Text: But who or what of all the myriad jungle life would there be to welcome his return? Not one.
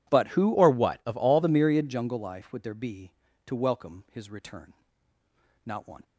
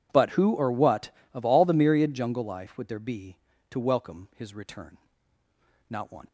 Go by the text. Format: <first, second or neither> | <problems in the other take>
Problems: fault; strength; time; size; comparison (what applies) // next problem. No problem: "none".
second | changes voice from "or" to "all"; from 0.5 to 1.4 s; 0.9 s long